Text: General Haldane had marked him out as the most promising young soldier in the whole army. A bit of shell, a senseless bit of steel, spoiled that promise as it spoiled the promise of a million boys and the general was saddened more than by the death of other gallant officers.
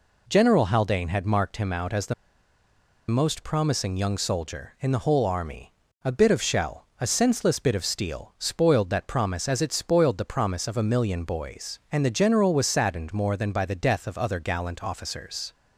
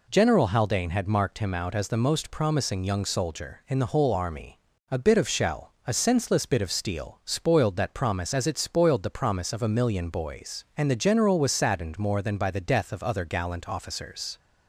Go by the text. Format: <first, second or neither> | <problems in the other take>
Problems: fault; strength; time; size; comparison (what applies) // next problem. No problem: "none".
second | pauses between "the" and "most"; noticeable; at 2.1 s; 0.94 s long